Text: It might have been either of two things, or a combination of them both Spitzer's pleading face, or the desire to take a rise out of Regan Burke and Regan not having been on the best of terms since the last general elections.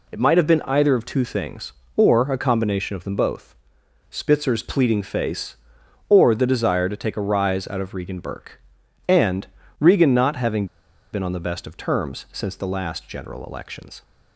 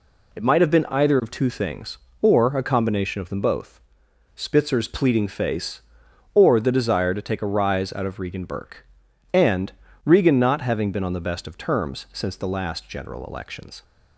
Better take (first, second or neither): second